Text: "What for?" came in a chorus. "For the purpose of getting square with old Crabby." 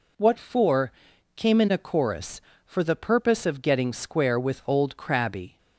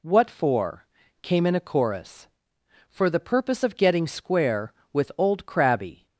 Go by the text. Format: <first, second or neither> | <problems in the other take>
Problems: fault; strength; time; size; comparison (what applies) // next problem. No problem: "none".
neither | none